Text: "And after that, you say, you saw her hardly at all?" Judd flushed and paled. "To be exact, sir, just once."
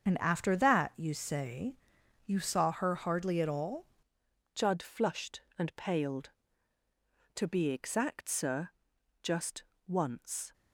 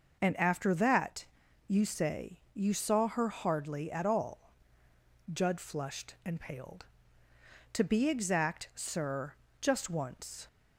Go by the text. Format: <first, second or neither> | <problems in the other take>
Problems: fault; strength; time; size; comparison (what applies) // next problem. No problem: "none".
second | starts louder than the rest; until 1.0 s; 7 dB // changes voice at "Judd"; from 4.5 s on; 6.0 s long // pauses between "just" and "once"; slight; at 9.6 s; 0.24 s long